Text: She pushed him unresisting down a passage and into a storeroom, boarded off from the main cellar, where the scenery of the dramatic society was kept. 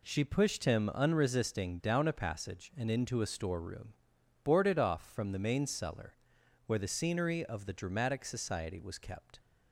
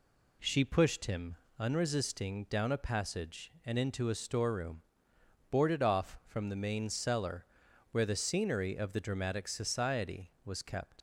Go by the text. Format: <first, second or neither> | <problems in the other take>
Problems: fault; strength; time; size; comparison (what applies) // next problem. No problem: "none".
first | pauses between "him" and "unresisting"; slight; at 1.3 s; 0.22 s long // leaves "kept" unfinished; at 10.9 s; 40 ms